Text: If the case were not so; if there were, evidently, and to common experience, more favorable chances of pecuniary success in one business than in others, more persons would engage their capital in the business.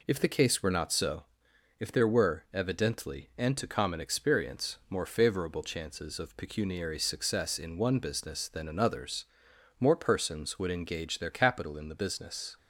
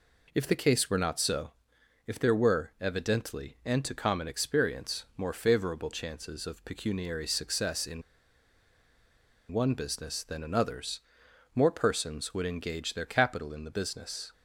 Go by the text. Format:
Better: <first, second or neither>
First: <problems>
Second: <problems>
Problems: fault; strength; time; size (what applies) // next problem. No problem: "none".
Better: first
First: none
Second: pauses between "in" and "one"; strong; at 8.0 s; 1.5 s long